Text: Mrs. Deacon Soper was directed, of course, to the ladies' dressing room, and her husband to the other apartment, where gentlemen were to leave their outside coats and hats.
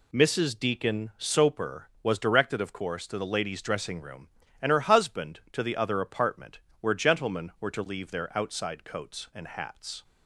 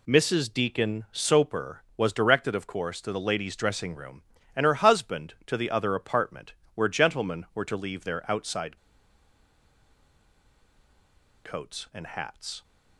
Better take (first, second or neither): first